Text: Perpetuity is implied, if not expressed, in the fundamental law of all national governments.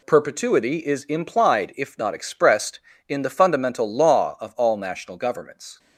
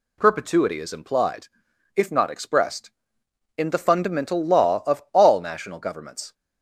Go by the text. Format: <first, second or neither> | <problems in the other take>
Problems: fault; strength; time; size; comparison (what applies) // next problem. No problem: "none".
neither | none